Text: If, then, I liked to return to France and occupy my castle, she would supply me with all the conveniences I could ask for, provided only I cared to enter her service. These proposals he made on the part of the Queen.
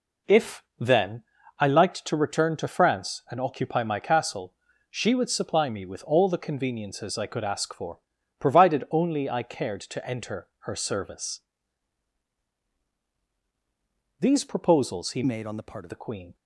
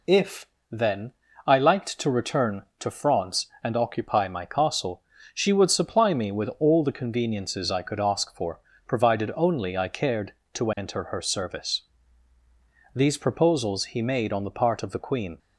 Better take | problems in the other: second | changes voice from "made" to "of"; from 15.2 to 15.8 s; 0.6 s long

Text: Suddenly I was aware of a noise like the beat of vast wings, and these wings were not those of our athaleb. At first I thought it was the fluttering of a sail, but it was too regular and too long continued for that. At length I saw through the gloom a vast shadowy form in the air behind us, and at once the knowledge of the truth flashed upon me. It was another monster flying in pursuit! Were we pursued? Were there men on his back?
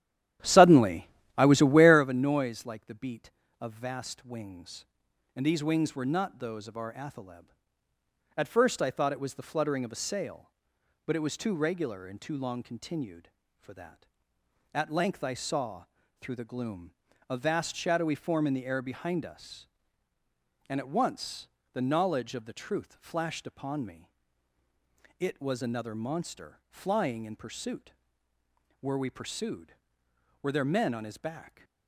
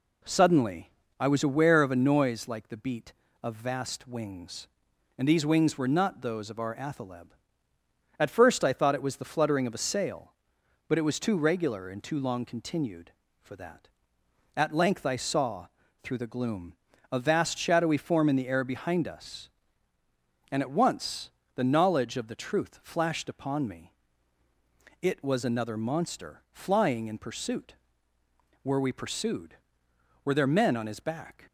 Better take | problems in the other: second | starts louder than the rest; strong; until 2.1 s; 11.5 dB // pauses between "Suddenly" and "I"; slight; at 1.0 s; 0.26 s long; slight in the second // pauses between "saw" and "through"; slight; at 15.8 s; 0.36 s long; slight in the second // pauses between "gloom" and "a"; slight; at 16.9 s; 0.36 s long; slight in the second // pauses between "once" and "the"; slight; at 21.4 s; 0.26 s long; slight in the second

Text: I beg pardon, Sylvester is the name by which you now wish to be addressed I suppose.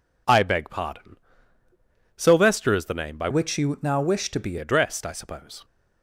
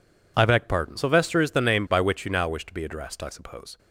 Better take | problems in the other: second | changes voice from "which" to "be"; from 3.2 to 4.5 s; 1.3 s long

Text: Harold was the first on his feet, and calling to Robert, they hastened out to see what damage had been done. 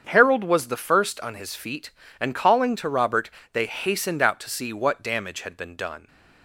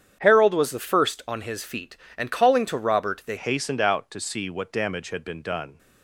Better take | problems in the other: first | starts louder than the rest; strong; until 1.2 s; 8.5 dB; strong in the first // changes voice at "hastened"; from 3.3 s on; 2.4 s long

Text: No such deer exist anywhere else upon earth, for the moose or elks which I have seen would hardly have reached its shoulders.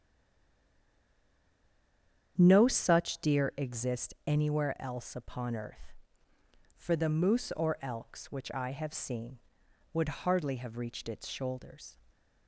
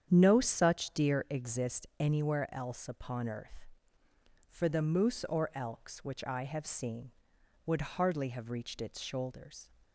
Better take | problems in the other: second | stays silent before the first word; until 2.3 s; 2.3 s long // starts louder than the rest; strong; until 3.4 s; 8.5 dB; strong in the second

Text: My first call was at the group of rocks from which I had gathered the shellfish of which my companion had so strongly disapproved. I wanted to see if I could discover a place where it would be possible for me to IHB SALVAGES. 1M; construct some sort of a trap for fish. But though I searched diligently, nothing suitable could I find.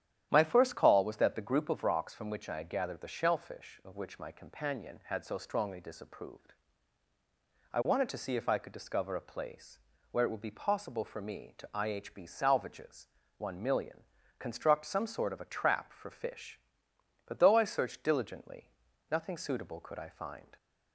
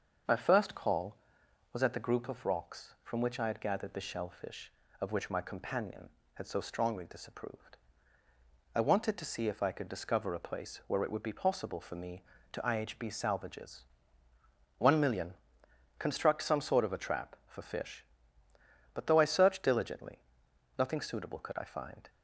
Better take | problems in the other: second | starts louder than the rest; strong; until 1.3 s; 10.5 dB; also in the second // says "that" for "at"; at 1.1 s // pauses between "place" and "where"; slight; at 9.7 s; 0.32 s long

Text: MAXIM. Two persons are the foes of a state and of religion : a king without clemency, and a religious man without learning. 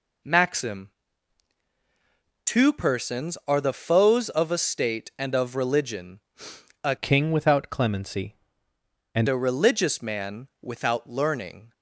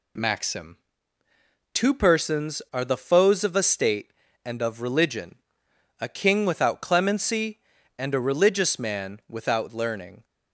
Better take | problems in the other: second | changes voice from "king" to "and"; from 6.9 to 9.2 s; 2.3 s long // pauses between "man" and "without"; slight; at 10.4 s; 0.16 s long

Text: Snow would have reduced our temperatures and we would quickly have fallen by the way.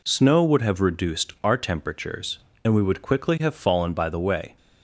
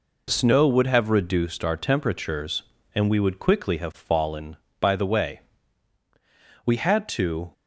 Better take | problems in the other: first | goes on to say "We had to"; noticeable; from 6.6 s on; 0.88 s long

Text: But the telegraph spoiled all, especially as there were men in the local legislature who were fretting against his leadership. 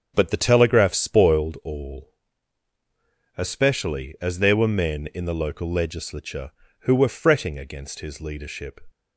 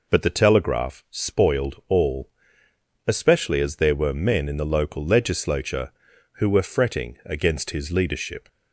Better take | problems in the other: second | starts louder than the rest; strong; until 1.5 s; 7 dB

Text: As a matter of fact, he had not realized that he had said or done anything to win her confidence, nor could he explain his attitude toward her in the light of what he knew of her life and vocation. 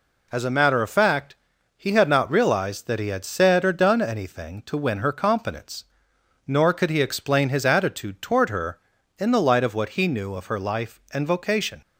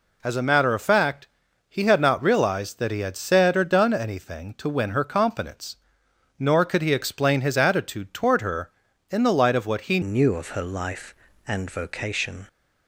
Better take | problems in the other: first | changes voice at "knew"; from 10.0 s on; 2.4 s long

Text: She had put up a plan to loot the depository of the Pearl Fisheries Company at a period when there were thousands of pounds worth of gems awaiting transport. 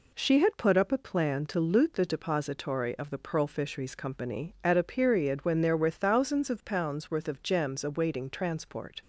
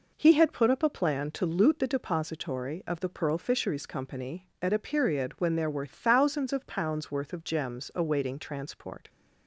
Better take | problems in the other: first | says "He" for "She"; at 0.1 s

